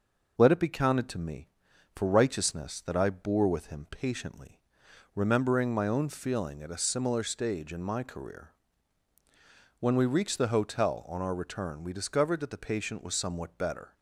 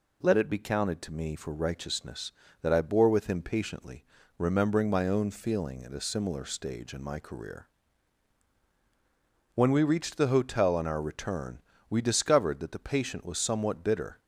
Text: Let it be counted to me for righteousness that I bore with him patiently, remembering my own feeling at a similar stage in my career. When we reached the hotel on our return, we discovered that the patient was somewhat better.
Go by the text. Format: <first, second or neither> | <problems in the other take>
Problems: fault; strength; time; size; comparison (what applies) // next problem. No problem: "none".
first | says "bitter" for "better"; at 13.8 s